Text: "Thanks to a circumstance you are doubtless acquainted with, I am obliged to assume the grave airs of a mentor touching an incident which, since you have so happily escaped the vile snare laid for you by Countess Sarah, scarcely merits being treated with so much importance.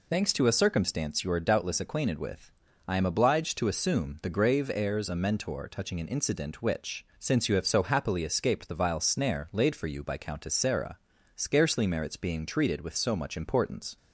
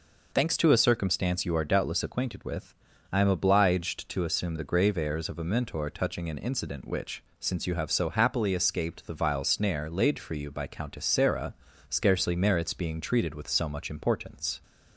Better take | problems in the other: second | skips "of"; at 5.1 s

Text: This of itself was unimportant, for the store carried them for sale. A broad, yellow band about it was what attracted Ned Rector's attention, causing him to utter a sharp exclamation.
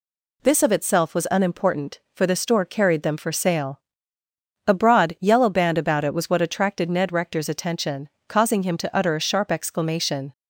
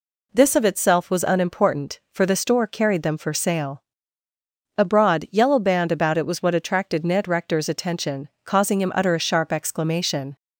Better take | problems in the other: first | skips "to"; at 8.9 s

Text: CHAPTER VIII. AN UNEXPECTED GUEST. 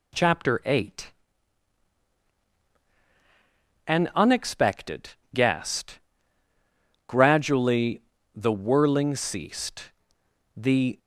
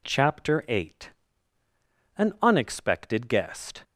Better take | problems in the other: second | pauses between "UNEXPECTED" and "GUEST"; slight; at 5.0 s; 0.24 s long // goes on to say "Gradually the whirling ceased the"; strong; from 7.0 s on; 3.9 s long

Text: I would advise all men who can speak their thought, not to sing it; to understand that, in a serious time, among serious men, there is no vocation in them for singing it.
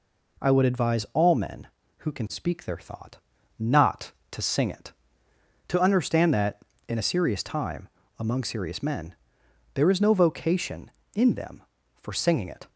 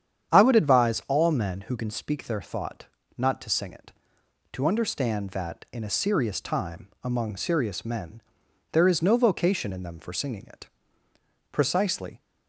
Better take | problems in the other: first | starts louder than the rest; strong; until 1.3 s; 8.5 dB // goes on to say "Precisely"; noticeable; from 11.5 s on; 0.70 s long

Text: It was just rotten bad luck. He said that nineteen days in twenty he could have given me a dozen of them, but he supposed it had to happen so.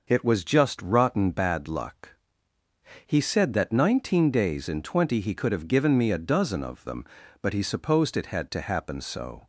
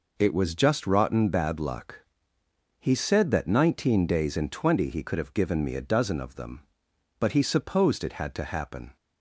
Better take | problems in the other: first | stops before "so"; at 8.9 s

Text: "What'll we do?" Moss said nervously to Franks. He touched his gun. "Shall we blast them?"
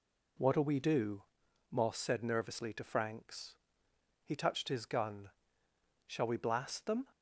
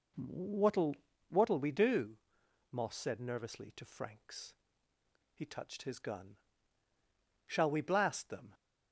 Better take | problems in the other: first | says "What'll" twice; at 1.2 s

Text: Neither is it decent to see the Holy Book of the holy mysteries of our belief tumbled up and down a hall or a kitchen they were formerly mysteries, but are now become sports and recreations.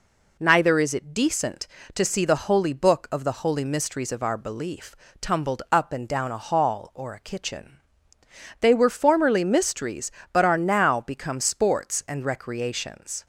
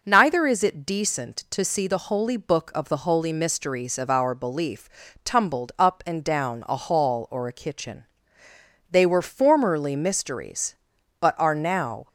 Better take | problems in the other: first | pauses between "belief" and "tumbled"; slight; at 4.8 s; 0.36 s long; slight in the first // pauses between "kitchen" and "they"; noticeable; at 8.0 s; 0.86 s long; noticeable in the first // stops before "become sports and recreations"; at 12.0 s

